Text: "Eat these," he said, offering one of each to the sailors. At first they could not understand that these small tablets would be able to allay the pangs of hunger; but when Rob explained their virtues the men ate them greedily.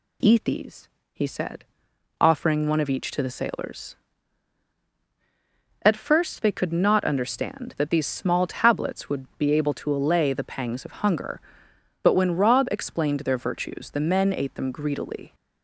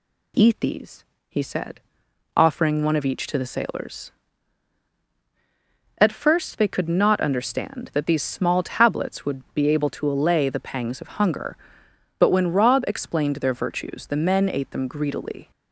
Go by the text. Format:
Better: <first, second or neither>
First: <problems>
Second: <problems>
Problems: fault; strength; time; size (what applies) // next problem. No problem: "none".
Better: neither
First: none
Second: none